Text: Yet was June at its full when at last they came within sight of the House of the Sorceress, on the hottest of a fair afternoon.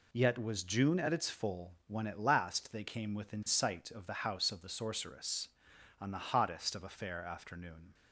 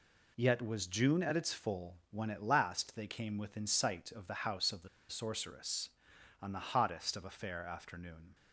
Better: first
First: none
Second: pauses between "the" and "Sorceress"; slight; at 4.8 s; 0.22 s long

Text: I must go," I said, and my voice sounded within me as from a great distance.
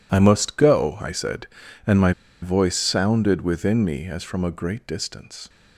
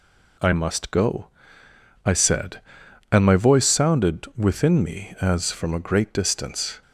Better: second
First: pauses between "my" and "voice"; slight; at 2.1 s; 0.29 s long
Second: none

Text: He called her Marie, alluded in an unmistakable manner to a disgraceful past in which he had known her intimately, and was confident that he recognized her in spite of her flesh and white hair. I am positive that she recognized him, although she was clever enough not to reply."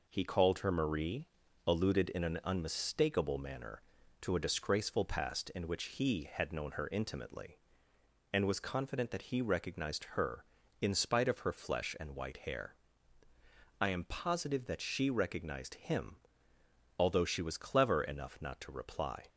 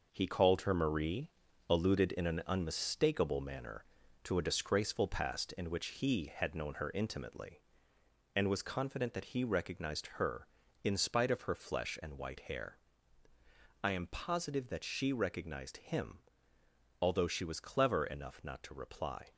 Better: first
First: none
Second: gets quieter; throughout; 6.5 dB

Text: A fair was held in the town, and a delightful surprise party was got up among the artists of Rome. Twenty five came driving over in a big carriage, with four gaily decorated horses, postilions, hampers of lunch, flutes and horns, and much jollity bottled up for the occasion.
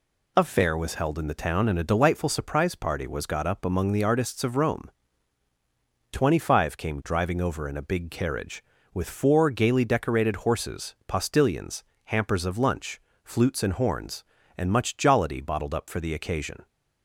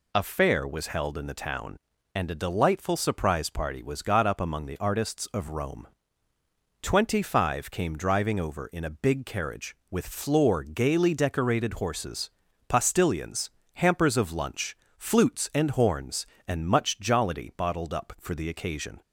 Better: first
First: none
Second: says "floor" for "four"; at 10.0 s

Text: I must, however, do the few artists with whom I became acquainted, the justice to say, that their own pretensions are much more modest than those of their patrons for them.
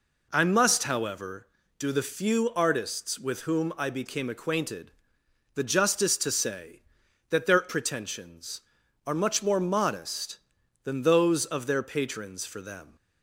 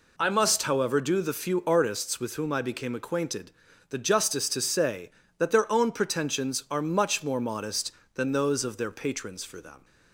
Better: second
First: skips "own"; at 7.6 s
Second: none

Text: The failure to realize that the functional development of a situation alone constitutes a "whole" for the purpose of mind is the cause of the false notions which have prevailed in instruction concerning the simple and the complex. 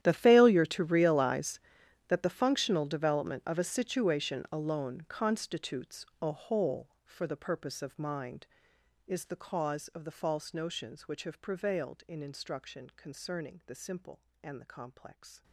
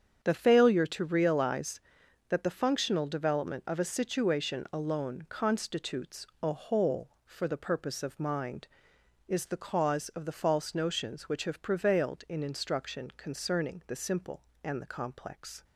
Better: second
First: gets quieter; strong; throughout; 20.5 dB // starts louder than the rest; strong; until 1.0 s; 11.5 dB // pauses between "constitutes" and "a"; slight; at 6.0 s; 0.16 s long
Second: starts louder than the rest; strong; until 1.2 s; 8 dB // pauses between "constitutes" and "a"; slight; at 6.2 s; 0.16 s long

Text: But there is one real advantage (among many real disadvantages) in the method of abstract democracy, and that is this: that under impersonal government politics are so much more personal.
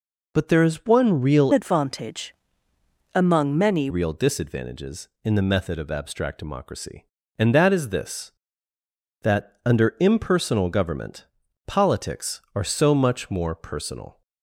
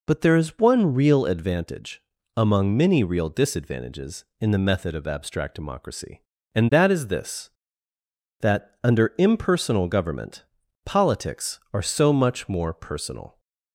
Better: second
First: changes voice from "advantage" to "many"; from 1.5 to 3.8 s; 2.3 s long // pauses between "government" and "politics"; at 11.2 s; 0.40 s long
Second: pauses between "government" and "politics"; at 10.4 s; 0.40 s long

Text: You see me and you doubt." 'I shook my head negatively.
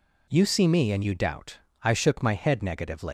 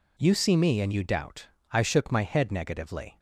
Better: second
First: leaves "negatively" unfinished; at 3.0 s; 175 ms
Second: none

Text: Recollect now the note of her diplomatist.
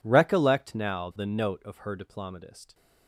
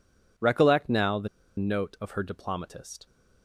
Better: first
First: none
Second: pauses between "the" and "note"; slight; at 1.2 s; 0.30 s long

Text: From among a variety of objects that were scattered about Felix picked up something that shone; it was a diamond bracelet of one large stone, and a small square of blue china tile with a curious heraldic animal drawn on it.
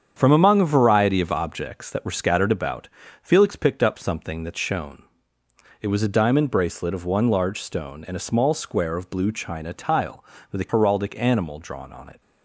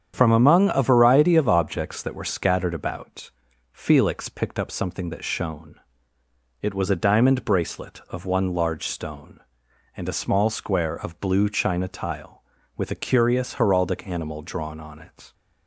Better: second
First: starts louder than the rest; strong; until 1.1 s; 8 dB // pauses between "about" and "Felix"; slight; at 2.8 s; 0.34 s long // skips "curious"; at 10.6 s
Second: starts louder than the rest; strong; until 1.1 s; 8.5 dB // pauses between "about" and "Felix"; at 3.3 s; 0.42 s long

